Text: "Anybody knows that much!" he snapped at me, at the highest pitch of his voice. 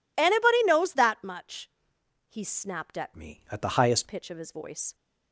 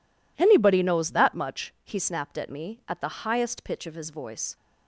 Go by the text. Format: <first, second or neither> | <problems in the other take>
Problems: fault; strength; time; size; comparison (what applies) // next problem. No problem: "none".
second | changes voice from "me" to "highest"; from 3.1 to 4.0 s; 0.9 s long